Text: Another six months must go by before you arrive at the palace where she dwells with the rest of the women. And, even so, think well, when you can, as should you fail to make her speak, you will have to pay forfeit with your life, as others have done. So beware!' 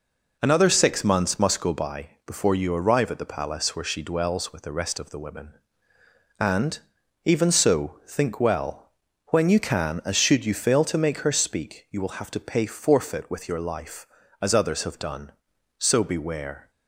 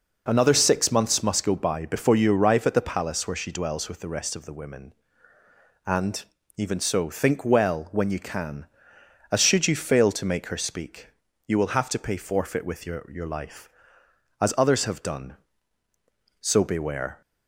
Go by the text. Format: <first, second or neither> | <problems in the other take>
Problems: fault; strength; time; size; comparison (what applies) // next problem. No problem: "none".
first | says "your" twice; at 13.0 s